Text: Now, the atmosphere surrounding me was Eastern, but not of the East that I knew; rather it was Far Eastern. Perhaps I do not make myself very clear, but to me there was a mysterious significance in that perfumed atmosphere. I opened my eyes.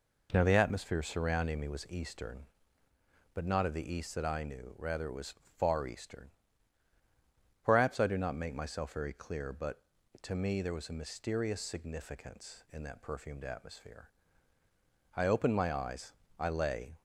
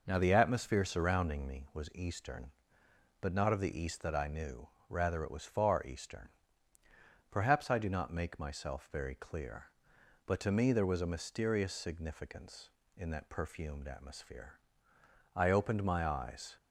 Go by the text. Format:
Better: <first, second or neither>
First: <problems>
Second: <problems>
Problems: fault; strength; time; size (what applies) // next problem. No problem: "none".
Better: second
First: pauses between "was" and "Far"; slight; at 5.3 s; 0.22 s long // goes on to say "I lay"; noticeable; from 16.3 s on; 0.62 s long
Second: none